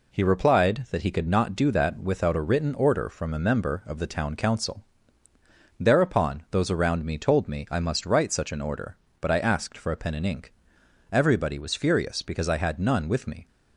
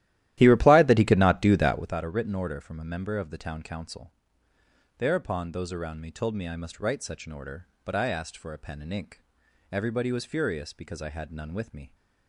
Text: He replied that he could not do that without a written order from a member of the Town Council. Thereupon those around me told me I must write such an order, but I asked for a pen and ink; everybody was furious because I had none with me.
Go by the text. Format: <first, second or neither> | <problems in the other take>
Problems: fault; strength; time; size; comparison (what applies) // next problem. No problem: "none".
first | starts louder than the rest; strong; until 2.0 s; 14 dB